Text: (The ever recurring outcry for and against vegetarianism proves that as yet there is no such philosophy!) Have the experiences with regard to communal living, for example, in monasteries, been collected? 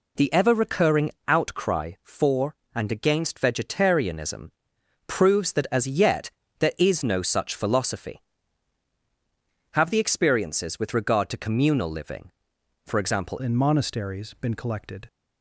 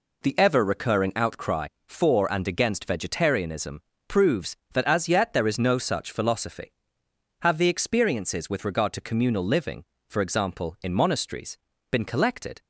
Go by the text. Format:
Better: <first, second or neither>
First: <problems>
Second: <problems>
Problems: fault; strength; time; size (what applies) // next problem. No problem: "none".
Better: second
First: pauses between "recurring" and "outcry"; slight; at 1.1 s; 0.16 s long // pauses between "vegetarianism" and "proves"; noticeable; at 4.5 s; 0.56 s long // pauses between "yet" and "there"; slight; at 6.3 s; 0.28 s long // changes voice at "in"; from 13.4 s on; 1.6 s long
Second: pauses between "vegetarianism" and "proves"; slight; at 3.8 s; 0.26 s long